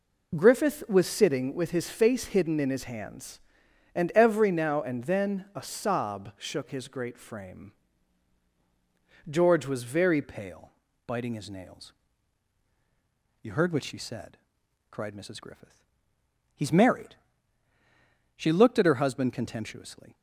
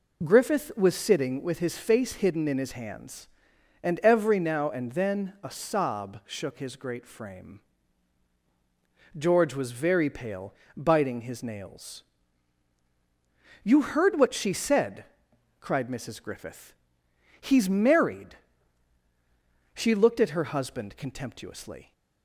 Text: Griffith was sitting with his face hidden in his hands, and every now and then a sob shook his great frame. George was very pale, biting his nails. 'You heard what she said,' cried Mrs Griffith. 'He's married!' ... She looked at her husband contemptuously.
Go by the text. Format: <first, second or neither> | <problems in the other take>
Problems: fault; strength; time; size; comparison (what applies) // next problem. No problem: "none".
second | changes voice at "pale"; from 10.2 s on; 9.9 s long